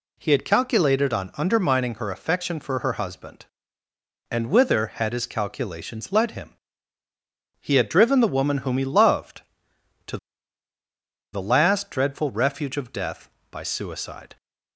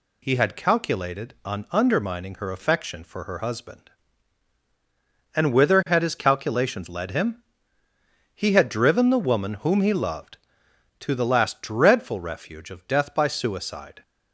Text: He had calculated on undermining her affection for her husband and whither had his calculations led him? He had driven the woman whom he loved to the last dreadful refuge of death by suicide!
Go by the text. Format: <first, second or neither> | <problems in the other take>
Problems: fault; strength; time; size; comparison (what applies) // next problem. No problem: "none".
second | pauses between "to" and "the"; at 10.1 s; 1.1 s long